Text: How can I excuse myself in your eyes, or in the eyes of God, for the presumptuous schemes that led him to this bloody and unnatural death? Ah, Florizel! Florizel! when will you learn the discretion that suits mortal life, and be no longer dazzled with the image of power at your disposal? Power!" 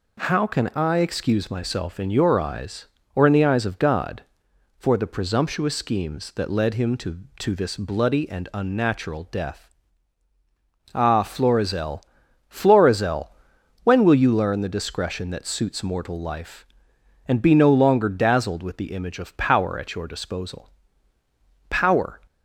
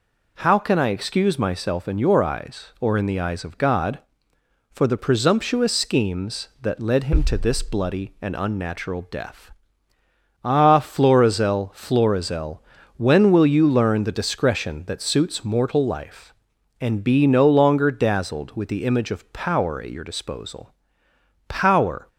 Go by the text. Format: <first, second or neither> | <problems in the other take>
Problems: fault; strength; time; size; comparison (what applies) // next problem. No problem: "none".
second | says "to" twice; at 7.3 s